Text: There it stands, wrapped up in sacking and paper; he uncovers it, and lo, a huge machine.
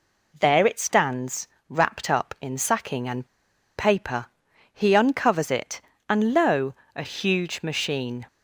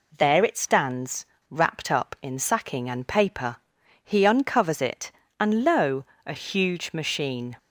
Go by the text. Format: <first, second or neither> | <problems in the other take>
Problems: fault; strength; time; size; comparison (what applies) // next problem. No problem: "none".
second | pauses between "and" and "paper"; noticeable; at 3.2 s; 0.51 s long